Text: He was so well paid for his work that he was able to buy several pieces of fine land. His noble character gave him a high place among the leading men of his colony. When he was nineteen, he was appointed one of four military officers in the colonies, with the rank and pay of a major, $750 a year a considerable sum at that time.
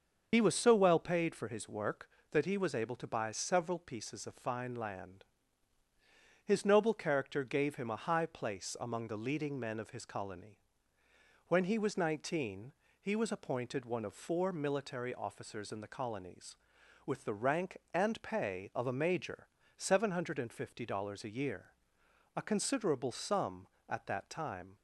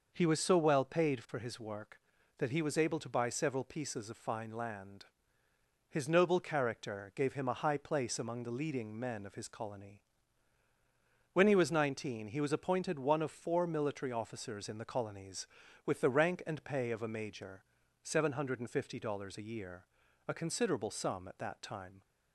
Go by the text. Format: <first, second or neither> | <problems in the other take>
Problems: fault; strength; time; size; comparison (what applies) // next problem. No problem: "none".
second | loses the start of "He"; at 0.3 s; 60 ms // starts louder than the rest; until 1.3 s; 6.5 dB // pauses between "year" and "a"; noticeable; at 21.6 s; 0.72 s long; also in the second